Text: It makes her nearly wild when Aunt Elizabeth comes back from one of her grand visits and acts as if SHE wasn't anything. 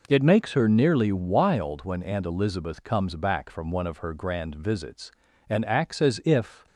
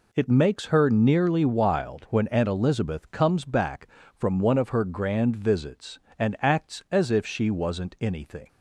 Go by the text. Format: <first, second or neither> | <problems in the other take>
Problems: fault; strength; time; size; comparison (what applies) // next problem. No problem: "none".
second | stops before "SHE wasn't anything"; at 6.6 s